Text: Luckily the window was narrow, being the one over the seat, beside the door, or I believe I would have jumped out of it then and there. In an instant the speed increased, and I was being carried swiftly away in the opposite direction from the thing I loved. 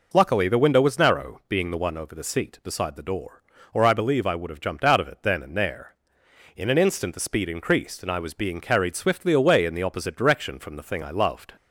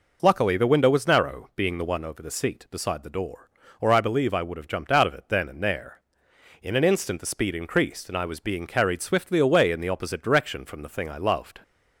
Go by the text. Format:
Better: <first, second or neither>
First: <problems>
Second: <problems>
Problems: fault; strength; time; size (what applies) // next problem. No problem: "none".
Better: neither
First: none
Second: none